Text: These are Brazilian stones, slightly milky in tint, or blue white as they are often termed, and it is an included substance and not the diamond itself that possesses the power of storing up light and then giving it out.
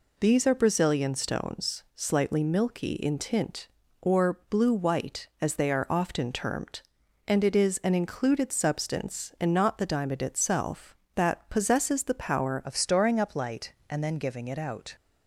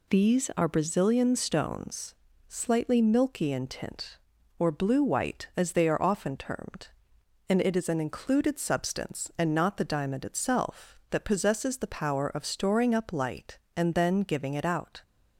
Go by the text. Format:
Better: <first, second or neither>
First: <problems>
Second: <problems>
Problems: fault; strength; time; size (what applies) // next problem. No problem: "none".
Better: second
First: changes voice at "of"; from 12.6 s on; 2.3 s long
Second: none